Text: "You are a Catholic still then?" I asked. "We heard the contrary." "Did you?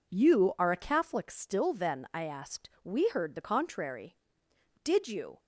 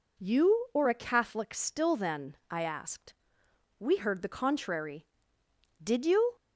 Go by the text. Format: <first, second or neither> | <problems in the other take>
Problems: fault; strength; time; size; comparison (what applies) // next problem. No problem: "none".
first | says "or" for "are"; at 0.7 s